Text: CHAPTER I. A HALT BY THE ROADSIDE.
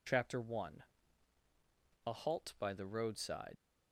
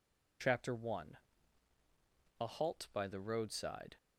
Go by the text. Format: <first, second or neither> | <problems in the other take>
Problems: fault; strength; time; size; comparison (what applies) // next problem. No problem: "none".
second | leaves "ROADSIDE" unfinished; at 3.5 s; 65 ms